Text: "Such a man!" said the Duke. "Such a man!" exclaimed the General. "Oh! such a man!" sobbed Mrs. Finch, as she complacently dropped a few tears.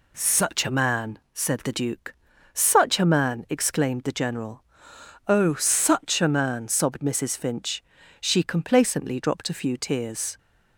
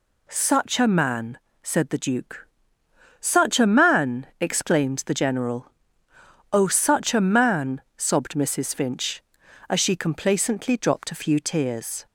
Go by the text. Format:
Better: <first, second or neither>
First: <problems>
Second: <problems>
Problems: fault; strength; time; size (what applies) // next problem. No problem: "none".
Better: second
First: skips "as"; at 8.0 s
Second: none